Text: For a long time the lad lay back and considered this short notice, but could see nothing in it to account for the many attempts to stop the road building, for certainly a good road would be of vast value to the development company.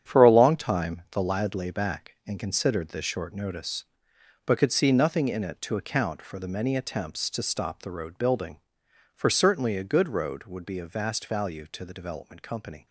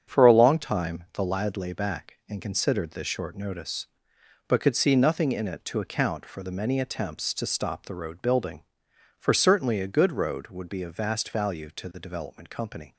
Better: second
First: gets quieter; strong; throughout; 9 dB // starts louder than the rest; strong; until 1.1 s; 8.5 dB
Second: starts louder than the rest; strong; until 1.1 s; 7.5 dB

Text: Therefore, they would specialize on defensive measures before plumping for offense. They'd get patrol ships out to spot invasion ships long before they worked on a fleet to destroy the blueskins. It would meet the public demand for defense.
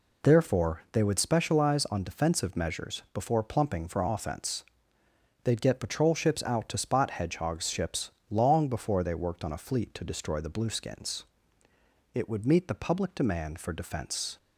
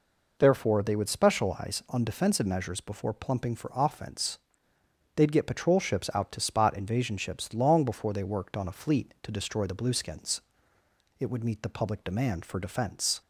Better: second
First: says "hedgehogs" for "invasion"; at 7.1 s // pauses between "ships" and "long"; slight; at 8.1 s; 0.18 s long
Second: none

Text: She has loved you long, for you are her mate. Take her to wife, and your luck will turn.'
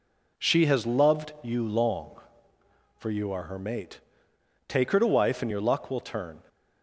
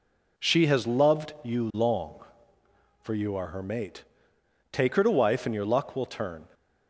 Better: neither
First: none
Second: none

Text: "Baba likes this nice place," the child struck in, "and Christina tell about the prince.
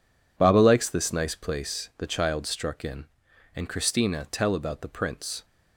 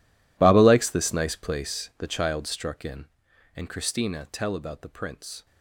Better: first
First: none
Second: gets quieter; strong; throughout; 19.5 dB

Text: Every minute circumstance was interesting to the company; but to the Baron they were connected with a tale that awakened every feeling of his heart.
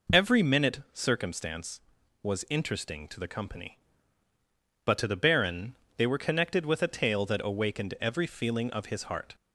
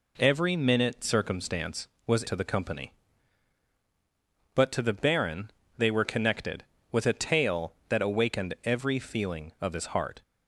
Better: first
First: pauses between "Baron" and "they"; slight; at 5.7 s; 0.20 s long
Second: skips "interesting"; at 2.2 s // pauses between "Baron" and "they"; slight; at 5.4 s; 0.26 s long

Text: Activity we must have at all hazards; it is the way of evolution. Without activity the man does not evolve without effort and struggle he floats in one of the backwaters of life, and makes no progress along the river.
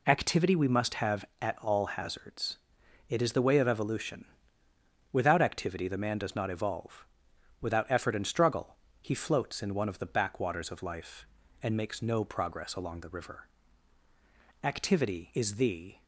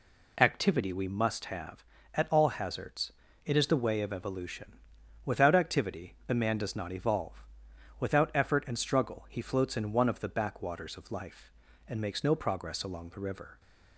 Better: second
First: pauses between "evolve" and "without"; noticeable; at 7.0 s; 0.56 s long // pauses between "struggle" and "he"; slight; at 8.7 s; 0.26 s long // goes on to say "Activity is the"; from 14.6 s on; 1.3 s long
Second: pauses between "evolve" and "without"; noticeable; at 7.4 s; 0.56 s long

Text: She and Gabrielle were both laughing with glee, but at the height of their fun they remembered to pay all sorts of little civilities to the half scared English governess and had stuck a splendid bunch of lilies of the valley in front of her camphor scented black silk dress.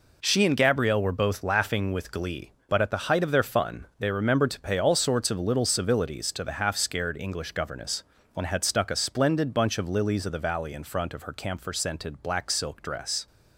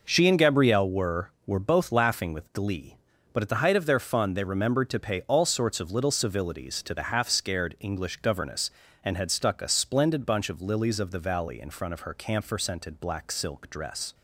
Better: first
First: none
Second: says "were" twice; at 1.4 s

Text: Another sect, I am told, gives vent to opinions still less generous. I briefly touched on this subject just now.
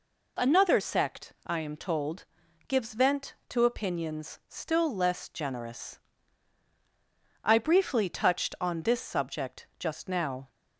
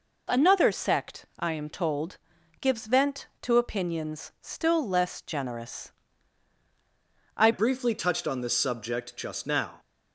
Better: first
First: none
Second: changes voice at "briefly"; from 7.5 s on; 2.2 s long

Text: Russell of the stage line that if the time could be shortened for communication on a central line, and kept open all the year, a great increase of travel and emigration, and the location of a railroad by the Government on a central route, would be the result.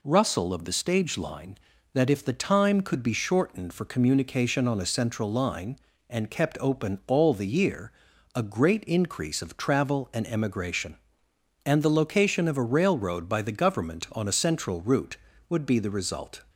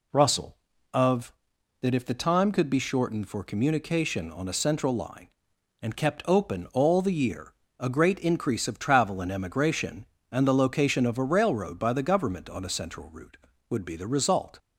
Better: first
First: none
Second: skips "the stage line"; at 1.5 s

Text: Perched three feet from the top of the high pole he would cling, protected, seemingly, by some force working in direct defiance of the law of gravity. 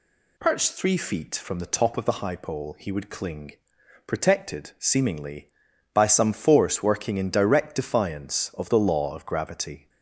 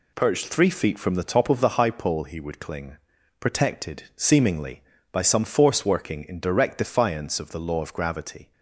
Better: neither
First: none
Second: none

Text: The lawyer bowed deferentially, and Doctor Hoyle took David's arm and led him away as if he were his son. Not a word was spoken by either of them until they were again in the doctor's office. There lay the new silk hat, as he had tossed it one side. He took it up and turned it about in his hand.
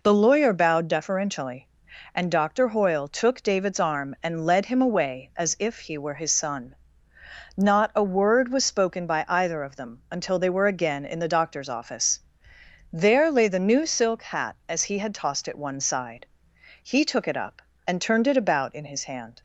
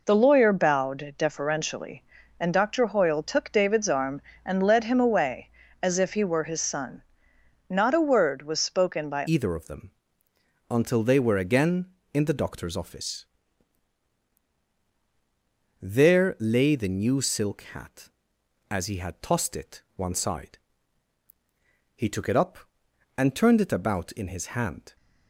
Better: first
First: none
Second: changes voice at "either"; from 9.2 s on; 15.7 s long // pauses between "them" and "until"; noticeable; at 9.8 s; 0.80 s long

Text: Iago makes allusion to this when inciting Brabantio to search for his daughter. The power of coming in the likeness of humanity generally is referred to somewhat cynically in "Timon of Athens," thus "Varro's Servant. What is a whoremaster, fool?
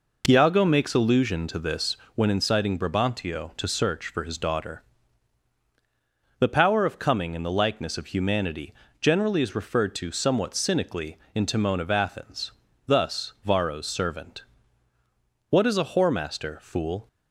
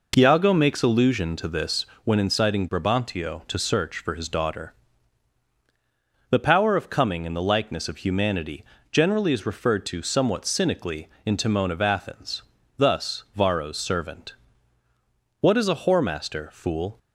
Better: neither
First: pauses between "this" and "when"; slight; at 1.9 s; 0.18 s long // pauses between "humanity" and "generally"; slight; at 8.7 s; 0.26 s long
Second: pauses between "this" and "when"; slight; at 1.8 s; 0.18 s long // pauses between "humanity" and "generally"; slight; at 8.6 s; 0.26 s long

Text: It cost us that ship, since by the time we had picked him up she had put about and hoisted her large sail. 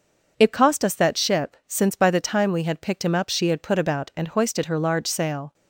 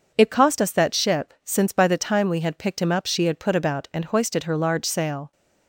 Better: neither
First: none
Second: none

